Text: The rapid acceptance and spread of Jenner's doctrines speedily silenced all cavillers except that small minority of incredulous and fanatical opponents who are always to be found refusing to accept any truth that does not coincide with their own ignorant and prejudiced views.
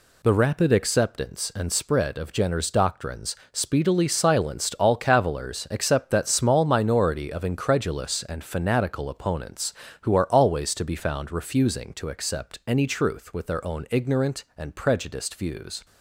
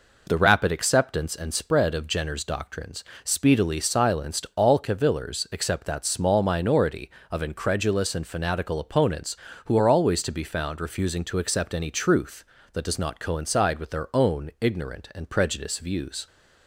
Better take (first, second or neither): second